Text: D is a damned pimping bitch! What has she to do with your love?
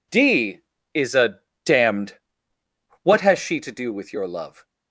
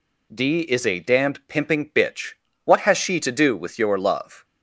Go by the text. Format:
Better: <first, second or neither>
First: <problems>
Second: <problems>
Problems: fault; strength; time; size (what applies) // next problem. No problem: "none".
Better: second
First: pauses between "a" and "damned"; slight; at 1.4 s; 0.26 s long // skips "pimping bitch"; at 2.5 s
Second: none